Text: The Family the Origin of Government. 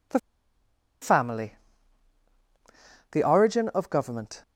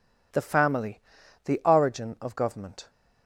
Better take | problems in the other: second | pauses between "The" and "Family"; noticeable; at 0.1 s; 0.82 s long // pauses between "Family" and "the"; strong; at 1.5 s; 1.5 s long; also in the second

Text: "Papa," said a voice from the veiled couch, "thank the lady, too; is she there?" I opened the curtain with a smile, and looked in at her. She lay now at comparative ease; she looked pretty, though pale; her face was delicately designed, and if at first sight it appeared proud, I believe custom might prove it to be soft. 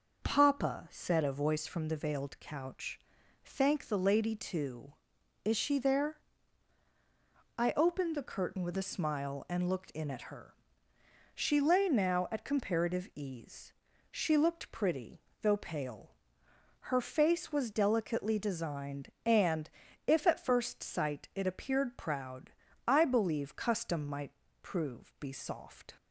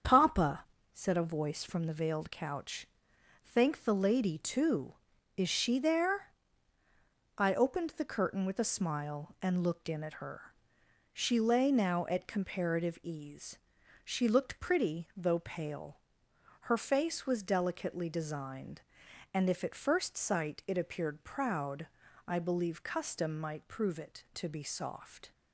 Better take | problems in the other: second | starts louder than the rest; noticeable; until 1.2 s; 6 dB; strong in the second // pauses between "and" and "if"; slight; at 19.7 s; 0.36 s long // pauses between "might" and "prove"; slight; at 24.3 s; 0.32 s long // skips "it to"; at 25.1 s

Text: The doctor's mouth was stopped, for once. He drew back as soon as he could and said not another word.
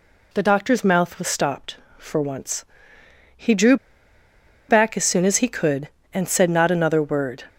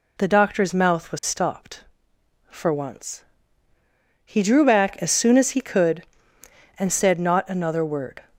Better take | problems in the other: second | pauses between "drew" and "back"; noticeable; at 3.7 s; 0.93 s long

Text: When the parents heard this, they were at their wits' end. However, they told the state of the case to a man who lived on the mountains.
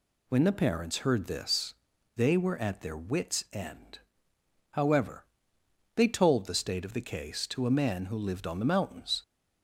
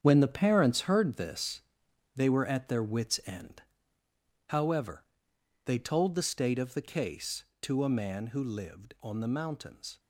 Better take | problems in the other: first | gets quieter; strong; throughout; 10.5 dB

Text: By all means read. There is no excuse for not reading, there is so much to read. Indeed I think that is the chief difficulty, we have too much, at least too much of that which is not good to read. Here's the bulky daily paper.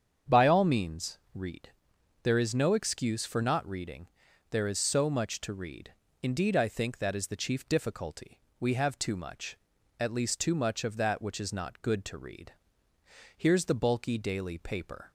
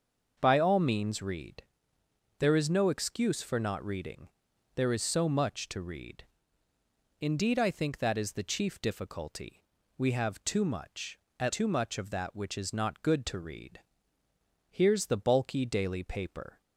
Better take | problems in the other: first | starts louder than the rest; until 1.4 s; 6.5 dB; strong in the first // skips "least"; at 11.5 s

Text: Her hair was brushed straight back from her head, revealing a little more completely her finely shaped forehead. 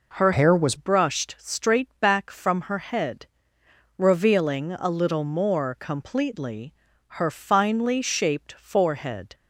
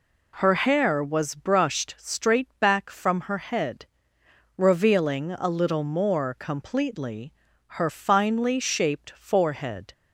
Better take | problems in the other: second | changes voice from "hair" to "was"; from 0.3 to 0.7 s; 0.4 s long // pauses between "completely" and "her"; noticeable; at 6.7 s; 0.46 s long; noticeable in the second

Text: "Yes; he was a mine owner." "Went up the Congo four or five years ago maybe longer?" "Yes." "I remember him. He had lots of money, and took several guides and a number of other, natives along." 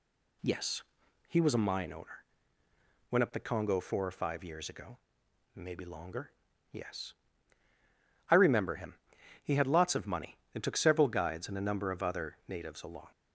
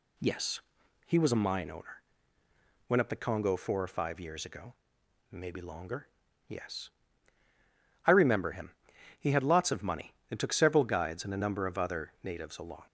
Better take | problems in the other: neither | pauses between "ago" and "maybe"; noticeable; the same in both

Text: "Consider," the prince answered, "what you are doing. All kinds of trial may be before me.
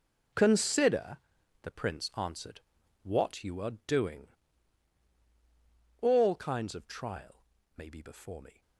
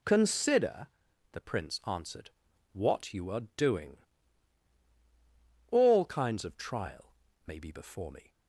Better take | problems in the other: second | gets quieter; strong; throughout; 13.5 dB // pauses between "trial" and "may"; slight; at 7.4 s; 0.32 s long; slight in the second

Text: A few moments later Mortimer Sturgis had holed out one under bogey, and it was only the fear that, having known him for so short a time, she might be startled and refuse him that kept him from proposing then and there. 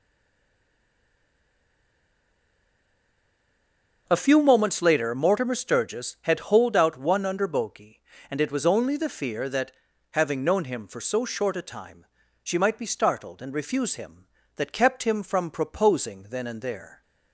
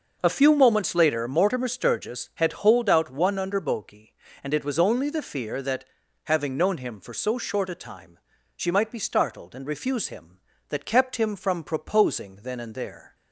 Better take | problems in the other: second | stays silent before the first word; strong; until 4.0 s; 4.0 s long

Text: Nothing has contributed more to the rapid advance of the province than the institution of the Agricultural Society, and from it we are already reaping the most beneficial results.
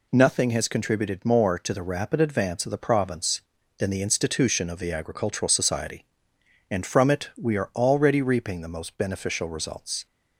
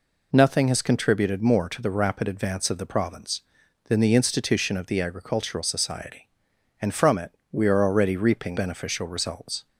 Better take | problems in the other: first | pauses between "it" and "we"; slight; at 7.3 s; 0.18 s long // skips "the most"; at 8.5 s

